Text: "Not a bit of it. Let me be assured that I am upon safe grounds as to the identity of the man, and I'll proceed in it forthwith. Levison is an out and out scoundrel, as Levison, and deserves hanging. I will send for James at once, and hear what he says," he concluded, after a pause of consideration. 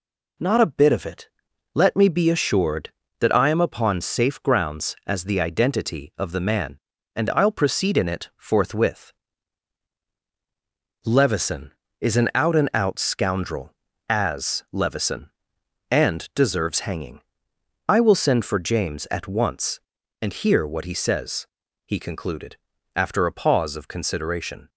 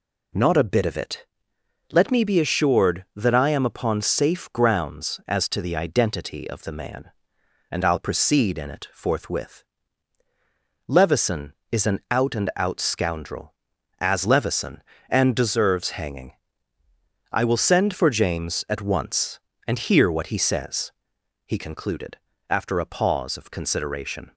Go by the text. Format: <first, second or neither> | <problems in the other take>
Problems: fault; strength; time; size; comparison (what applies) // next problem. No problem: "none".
second | skips "to"; at 5.2 s